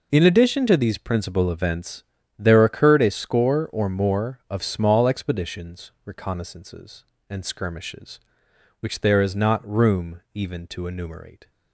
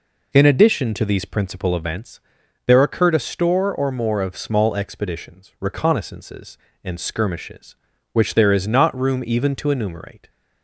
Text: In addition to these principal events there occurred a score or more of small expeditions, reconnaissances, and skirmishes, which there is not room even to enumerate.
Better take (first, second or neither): first